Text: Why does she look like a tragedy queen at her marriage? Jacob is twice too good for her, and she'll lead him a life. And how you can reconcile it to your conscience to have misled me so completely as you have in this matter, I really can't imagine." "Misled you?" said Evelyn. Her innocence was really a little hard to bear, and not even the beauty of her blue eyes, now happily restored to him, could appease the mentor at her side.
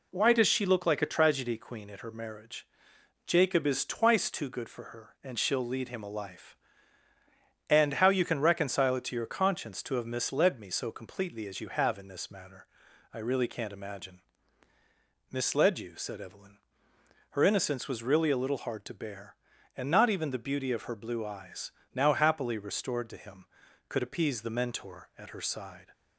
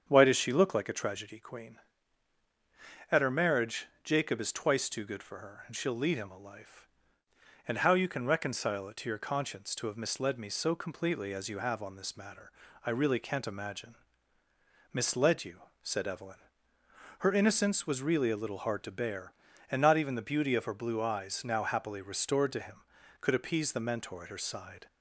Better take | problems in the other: first | starts louder than the rest; strong; until 1.0 s; 7.5 dB // says "on" for "in"; at 11.8 s

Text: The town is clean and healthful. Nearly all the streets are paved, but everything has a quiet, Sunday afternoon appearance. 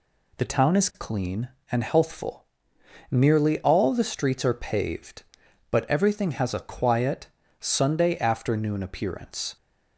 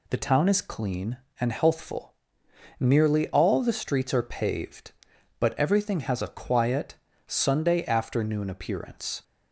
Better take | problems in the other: neither | none

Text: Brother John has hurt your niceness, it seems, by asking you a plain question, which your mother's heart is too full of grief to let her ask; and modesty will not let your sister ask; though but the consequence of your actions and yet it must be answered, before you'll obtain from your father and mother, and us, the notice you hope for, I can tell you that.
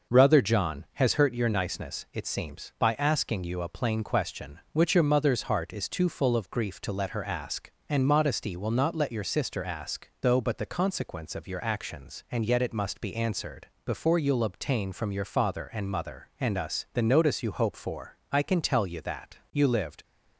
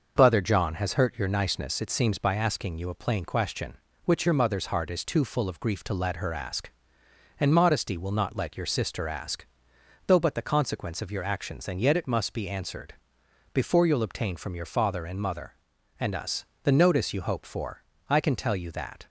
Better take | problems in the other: second | goes on to say "You lived"; from 19.5 s on; 0.50 s long

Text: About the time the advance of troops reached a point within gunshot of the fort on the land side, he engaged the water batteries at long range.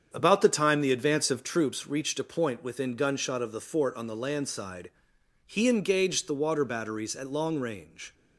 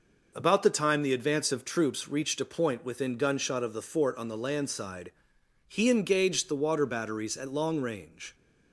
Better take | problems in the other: second | starts louder than the rest; strong; until 1.7 s; 7.5 dB

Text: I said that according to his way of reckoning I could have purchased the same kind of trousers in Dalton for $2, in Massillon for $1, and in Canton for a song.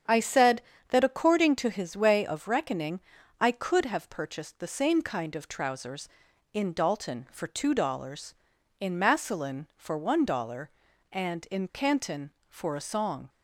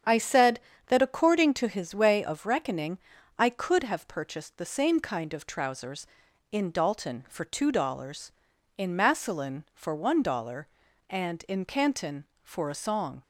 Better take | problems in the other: neither | starts louder than the rest; strong; the same in both // pauses between "reckoning" and "I"; the same in both

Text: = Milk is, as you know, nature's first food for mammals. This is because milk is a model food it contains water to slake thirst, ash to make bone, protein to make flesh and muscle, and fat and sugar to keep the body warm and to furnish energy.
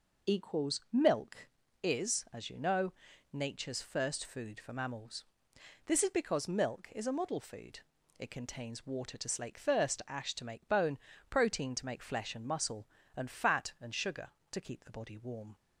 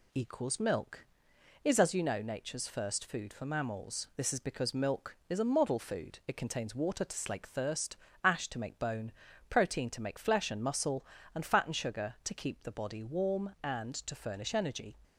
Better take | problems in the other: second | pauses between "food" and "it"; slight; at 7.8 s; 0.36 s long // stops before "and to furnish energy"; at 15.5 s

